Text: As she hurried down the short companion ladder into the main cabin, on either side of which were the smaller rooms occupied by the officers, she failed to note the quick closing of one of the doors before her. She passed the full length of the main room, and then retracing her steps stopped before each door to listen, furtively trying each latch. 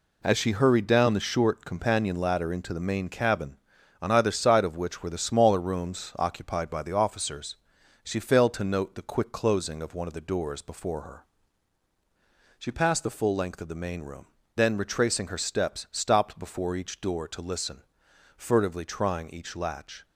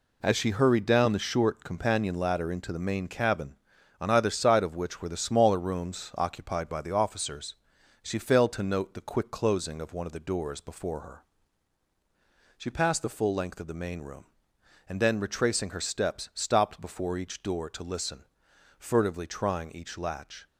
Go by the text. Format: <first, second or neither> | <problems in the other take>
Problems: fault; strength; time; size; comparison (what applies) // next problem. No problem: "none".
second | skips "and"; at 14.4 s